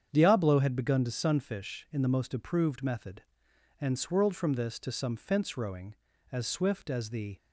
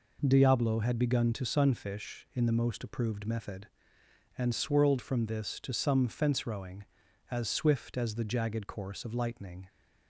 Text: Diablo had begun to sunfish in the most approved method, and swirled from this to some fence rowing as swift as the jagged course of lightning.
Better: second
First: starts louder than the rest; strong; until 1.1 s; 8 dB // stops before "jagged course of lightning"; at 7.3 s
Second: none

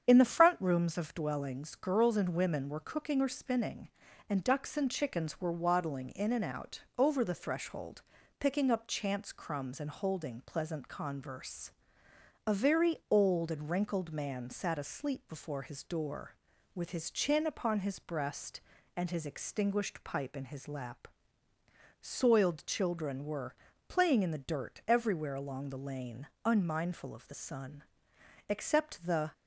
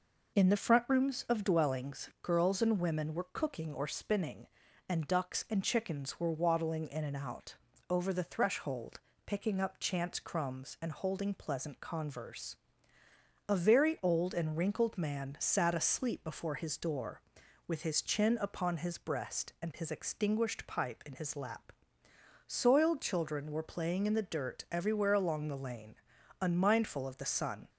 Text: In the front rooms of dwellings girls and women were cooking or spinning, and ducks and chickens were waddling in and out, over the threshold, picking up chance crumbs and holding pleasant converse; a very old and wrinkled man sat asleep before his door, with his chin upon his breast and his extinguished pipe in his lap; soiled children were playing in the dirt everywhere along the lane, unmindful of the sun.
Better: second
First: starts louder than the rest; strong; until 1.0 s; 8 dB // pauses between "were" and "playing"; slight; at 23.5 s; 0.34 s long // goes on to say "Except the"; noticeable; from 28.4 s on; 0.84 s long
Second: none

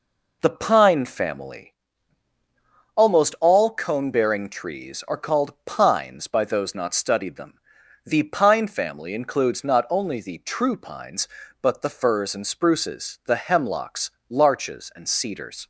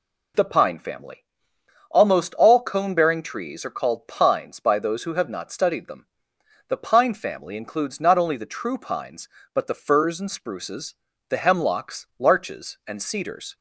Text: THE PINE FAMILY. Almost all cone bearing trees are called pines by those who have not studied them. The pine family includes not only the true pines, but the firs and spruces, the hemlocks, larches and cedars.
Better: second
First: skips "who have"; at 6.7 s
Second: none

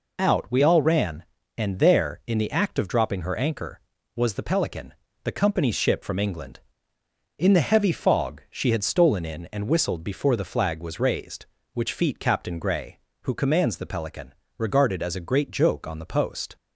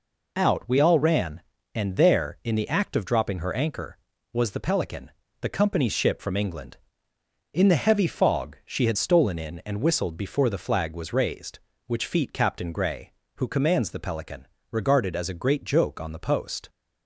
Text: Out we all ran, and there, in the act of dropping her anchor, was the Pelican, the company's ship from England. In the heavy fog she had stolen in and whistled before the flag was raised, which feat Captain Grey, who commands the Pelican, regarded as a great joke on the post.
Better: neither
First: none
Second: none

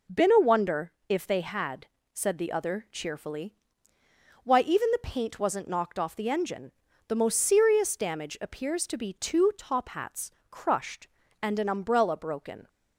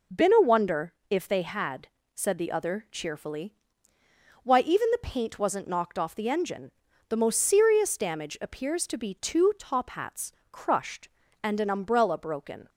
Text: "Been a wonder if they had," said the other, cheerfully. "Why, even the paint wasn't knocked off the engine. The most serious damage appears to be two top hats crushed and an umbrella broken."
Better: neither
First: pauses between "wonder" and "if"; slight; at 0.9 s; 0.16 s long // pauses between "hats" and "crushed"; slight; at 10.2 s; 0.20 s long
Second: pauses between "wonder" and "if"; slight; at 0.9 s; 0.16 s long // pauses between "hats" and "crushed"; slight; at 10.3 s; 0.20 s long

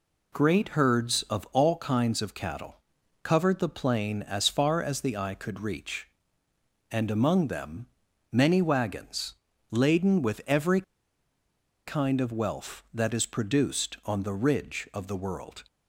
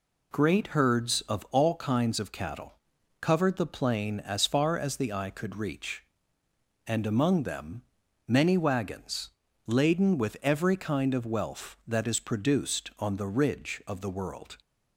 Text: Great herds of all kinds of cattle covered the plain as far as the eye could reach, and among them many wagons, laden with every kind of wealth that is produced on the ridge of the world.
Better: second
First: pauses between "cattle" and "covered"; at 2.7 s; 0.44 s long // pauses between "them" and "many"; noticeable; at 7.8 s; 0.46 s long // pauses between "every" and "kind"; at 10.8 s; 1.0 s long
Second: pauses between "cattle" and "covered"; at 2.7 s; 0.44 s long // pauses between "them" and "many"; noticeable; at 7.8 s; 0.46 s long

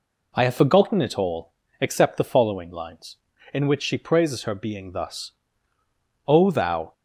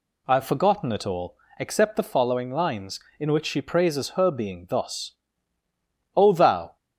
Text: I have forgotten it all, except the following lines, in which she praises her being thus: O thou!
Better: neither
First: none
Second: none

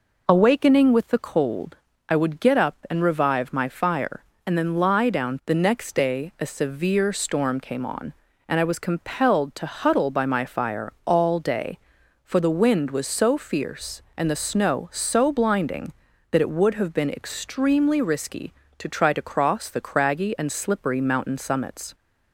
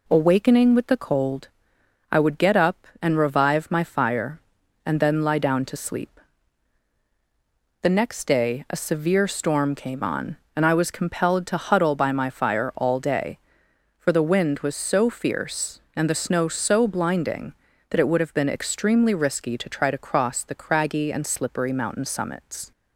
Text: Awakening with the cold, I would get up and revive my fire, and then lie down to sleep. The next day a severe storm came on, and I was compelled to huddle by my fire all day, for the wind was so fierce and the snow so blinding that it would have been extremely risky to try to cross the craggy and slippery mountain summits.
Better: second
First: skips "to sleep"; at 5.4 s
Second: none

